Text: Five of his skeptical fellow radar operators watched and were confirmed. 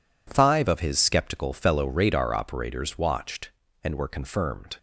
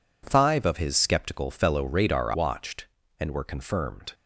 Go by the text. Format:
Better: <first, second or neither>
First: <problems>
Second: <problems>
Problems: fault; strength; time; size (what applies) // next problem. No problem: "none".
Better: first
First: none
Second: skips "operators"; at 2.3 s